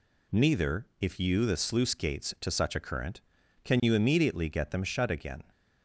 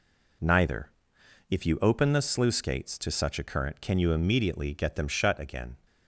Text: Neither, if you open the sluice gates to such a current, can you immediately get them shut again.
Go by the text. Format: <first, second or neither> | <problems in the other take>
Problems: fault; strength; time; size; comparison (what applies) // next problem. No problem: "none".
second | skips "open"; at 1.4 s